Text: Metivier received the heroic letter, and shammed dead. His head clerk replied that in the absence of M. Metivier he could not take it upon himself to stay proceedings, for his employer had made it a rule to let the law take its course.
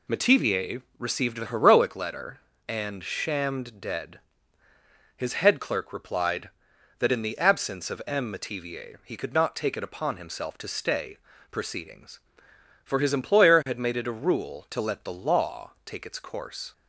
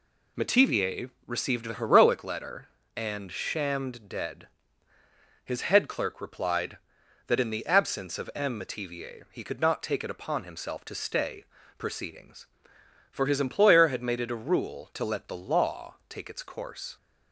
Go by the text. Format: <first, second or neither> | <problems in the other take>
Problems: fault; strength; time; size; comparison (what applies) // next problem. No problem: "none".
neither | pauses between "Metivier" and "received"; slight; the same in both // pauses between "stay" and "proceedings"; slight; the same in both